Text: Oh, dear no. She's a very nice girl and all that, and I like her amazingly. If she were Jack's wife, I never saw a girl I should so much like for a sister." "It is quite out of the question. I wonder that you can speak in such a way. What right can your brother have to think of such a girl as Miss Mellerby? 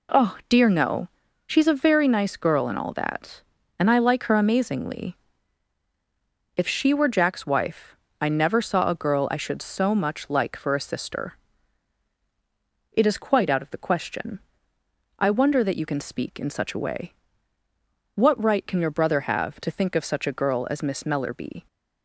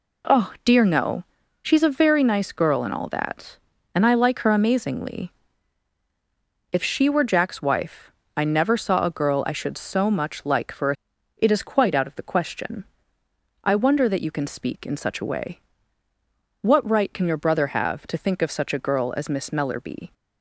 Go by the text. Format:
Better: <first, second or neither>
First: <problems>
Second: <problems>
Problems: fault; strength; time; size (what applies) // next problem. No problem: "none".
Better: first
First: none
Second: skips "sister"; at 11.1 s